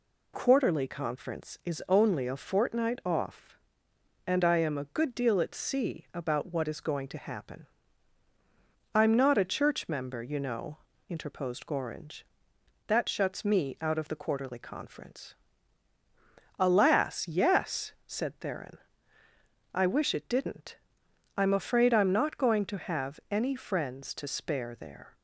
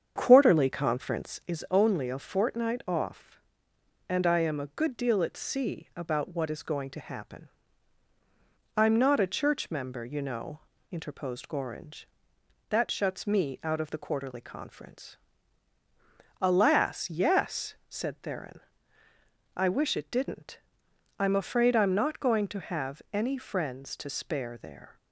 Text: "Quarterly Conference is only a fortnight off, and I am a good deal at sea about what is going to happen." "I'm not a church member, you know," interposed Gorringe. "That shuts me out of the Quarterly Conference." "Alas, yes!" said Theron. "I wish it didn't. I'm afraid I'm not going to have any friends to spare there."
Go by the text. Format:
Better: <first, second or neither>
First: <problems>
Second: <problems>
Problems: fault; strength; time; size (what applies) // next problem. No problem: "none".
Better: first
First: none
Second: starts louder than the rest; strong; until 1.5 s; 7.5 dB